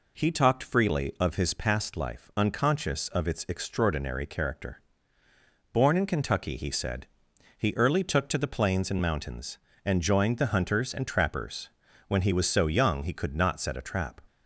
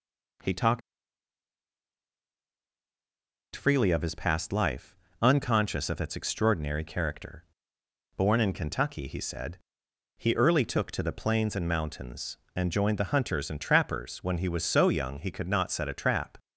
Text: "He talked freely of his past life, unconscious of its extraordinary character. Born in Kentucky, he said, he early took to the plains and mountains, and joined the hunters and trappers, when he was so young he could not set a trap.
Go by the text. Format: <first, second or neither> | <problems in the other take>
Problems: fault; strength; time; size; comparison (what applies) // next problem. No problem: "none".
first | pauses between "talked" and "freely"; strong; at 0.8 s; 2.7 s long